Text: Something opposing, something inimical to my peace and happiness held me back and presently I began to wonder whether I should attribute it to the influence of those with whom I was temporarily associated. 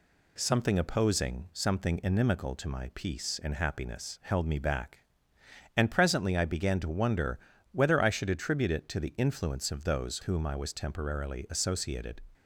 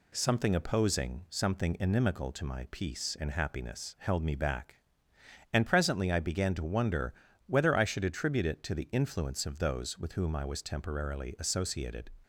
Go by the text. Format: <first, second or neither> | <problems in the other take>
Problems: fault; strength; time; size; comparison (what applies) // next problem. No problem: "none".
second | pauses between "wonder" and "whether"; slight; at 7.3 s; 0.32 s long; slight in the second // skips "with"; at 10.2 s